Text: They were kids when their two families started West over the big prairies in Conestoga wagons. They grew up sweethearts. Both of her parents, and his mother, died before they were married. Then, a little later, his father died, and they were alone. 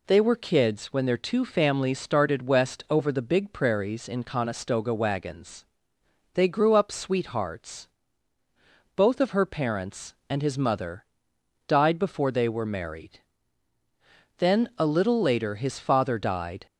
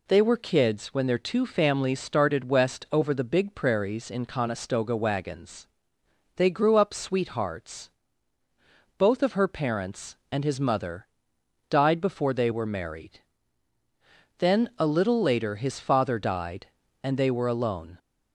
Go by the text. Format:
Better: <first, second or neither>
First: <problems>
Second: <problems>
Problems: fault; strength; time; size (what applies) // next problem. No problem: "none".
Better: second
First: stops before "and they were alone"; at 16.6 s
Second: none